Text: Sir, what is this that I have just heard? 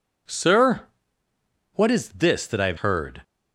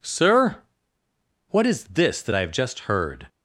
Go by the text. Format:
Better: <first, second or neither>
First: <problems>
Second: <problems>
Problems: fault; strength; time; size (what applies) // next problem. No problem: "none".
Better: second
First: skips "just"; at 2.7 s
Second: none